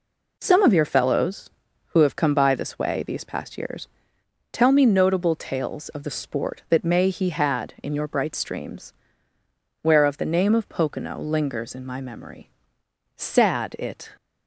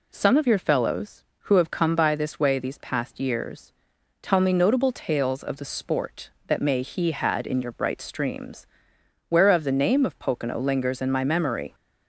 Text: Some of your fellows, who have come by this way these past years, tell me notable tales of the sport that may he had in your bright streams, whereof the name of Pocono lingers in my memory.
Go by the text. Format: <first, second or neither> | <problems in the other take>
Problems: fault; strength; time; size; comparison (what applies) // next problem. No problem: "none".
second | goes on to say "Sad it"; noticeable; from 13.1 s on; 1.0 s long